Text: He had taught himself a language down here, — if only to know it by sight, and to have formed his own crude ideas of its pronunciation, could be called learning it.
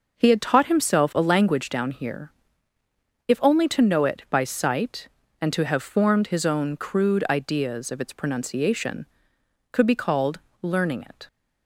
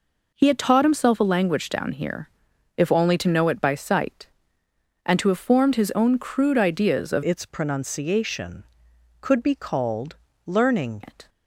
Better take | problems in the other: first | changes voice from "its" to "learning"; from 7.2 to 11.0 s; 3.8 s long // pauses between "called" and "learning"; slight; at 10.1 s; 0.30 s long; slight in the first

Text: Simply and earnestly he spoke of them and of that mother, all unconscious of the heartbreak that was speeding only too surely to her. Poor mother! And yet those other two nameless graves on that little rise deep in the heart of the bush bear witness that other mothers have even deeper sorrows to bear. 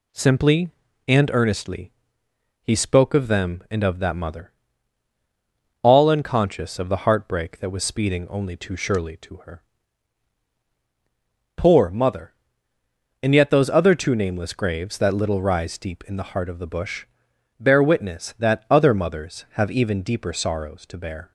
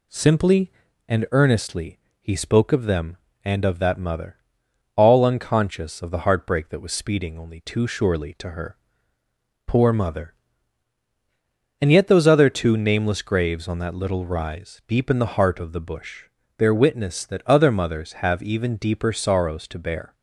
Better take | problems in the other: second | pauses between "earnestly" and "he"; noticeable; at 1.9 s; 0.70 s long; slight in the second // skips "on"; at 14.9 s // pauses between "bush" and "bear"; noticeable; at 17.0 s; 0.54 s long; slight in the second

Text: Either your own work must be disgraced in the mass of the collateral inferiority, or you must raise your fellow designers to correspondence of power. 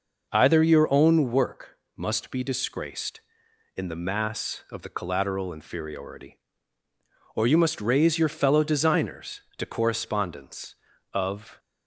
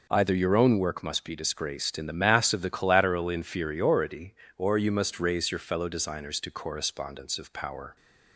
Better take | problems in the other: second | pauses between "work" and "must"; slight; at 1.7 s; 0.18 s long // stops before "power"; at 11.5 s

